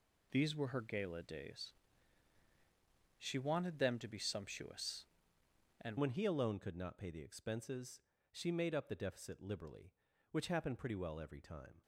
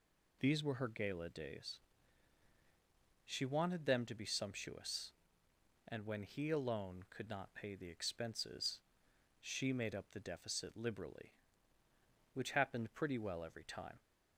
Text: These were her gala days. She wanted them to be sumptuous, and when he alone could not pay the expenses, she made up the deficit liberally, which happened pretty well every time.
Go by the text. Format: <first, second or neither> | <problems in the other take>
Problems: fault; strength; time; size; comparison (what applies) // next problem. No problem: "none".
second | changes voice at "when"; from 5.9 s on; 5.9 s long